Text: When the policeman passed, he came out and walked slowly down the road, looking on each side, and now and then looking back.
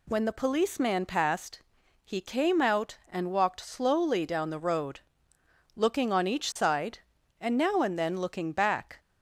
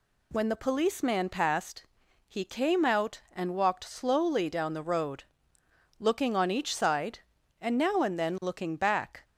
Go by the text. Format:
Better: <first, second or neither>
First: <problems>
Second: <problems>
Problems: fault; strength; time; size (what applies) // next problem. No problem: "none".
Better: neither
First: none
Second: none